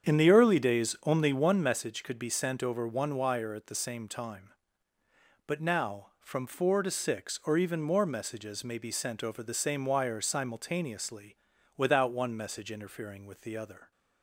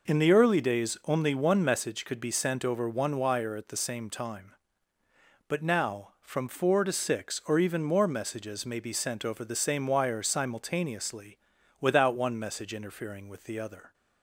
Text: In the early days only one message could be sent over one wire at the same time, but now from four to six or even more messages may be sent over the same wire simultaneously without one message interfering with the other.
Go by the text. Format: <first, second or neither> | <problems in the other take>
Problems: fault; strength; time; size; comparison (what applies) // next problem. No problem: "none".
second | starts louder than the rest; strong; until 1.6 s; 8 dB // pauses between "simultaneously" and "without"; at 11.3 s; 0.40 s long; also in the second